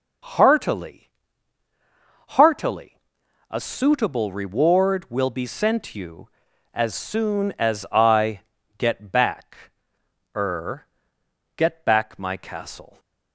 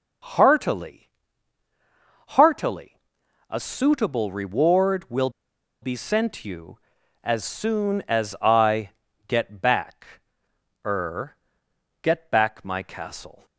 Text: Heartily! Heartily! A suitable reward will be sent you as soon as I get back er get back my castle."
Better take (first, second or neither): first